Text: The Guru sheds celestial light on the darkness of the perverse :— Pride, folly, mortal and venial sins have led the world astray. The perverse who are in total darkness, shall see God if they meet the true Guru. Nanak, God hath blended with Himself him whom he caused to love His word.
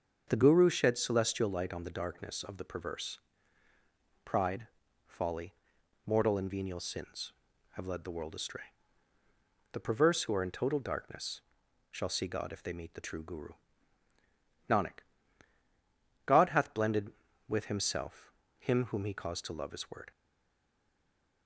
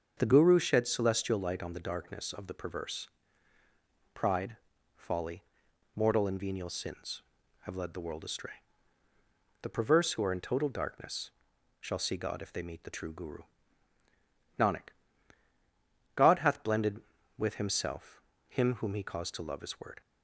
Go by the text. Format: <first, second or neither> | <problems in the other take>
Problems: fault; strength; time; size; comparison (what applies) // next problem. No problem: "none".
second | starts louder than the rest; until 1.2 s; 6.5 dB; also in the second // pauses between "Himself" and "him"; slight; at 18.3 s; 0.28 s long; slight in the second // stays silent after the last word; noticeable; from 20.1 s on; 1.3 s long